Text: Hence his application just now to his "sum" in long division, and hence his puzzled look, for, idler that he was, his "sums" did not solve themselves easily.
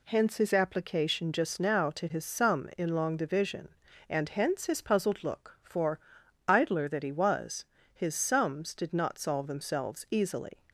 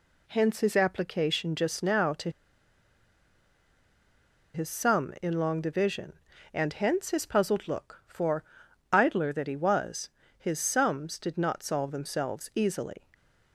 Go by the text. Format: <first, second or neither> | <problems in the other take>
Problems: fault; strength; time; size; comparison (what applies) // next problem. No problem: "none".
first | pauses between "to" and "his"; strong; at 2.2 s; 2.2 s long